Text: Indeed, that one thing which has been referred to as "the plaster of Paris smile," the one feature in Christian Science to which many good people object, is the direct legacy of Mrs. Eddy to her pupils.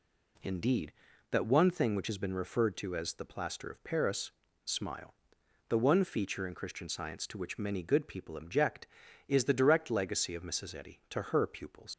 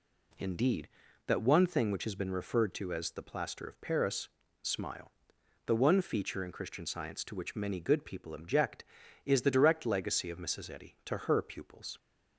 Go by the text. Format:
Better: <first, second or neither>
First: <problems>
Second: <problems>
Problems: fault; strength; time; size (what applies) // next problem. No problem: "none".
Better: second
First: pauses between "Paris" and "smile"; slight; at 4.3 s; 0.32 s long // leaves "pupils" unfinished; at 11.9 s; 90 ms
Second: pauses between "Paris" and "smile"; slight; at 4.3 s; 0.32 s long